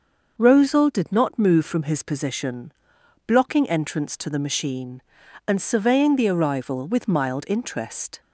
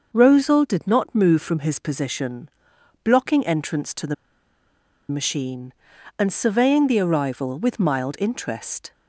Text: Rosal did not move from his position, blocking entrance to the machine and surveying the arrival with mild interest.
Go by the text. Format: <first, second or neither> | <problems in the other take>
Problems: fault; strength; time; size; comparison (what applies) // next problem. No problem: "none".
first | starts louder than the rest; noticeable; until 1.1 s; 6 dB; noticeable in the first // pauses between "the" and "machine"; noticeable; at 4.1 s; 0.95 s long